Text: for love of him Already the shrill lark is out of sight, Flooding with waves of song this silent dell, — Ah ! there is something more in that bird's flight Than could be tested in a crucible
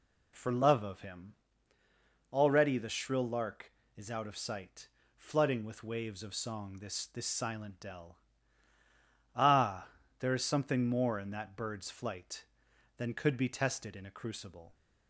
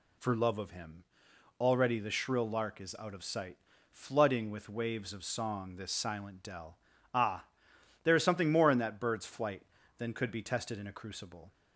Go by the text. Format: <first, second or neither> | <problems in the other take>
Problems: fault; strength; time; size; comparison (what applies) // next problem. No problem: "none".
second | pauses between "him" and "Already"; noticeable; at 1.3 s; 0.98 s long; noticeable in the second // says "this" twice; at 7.0 s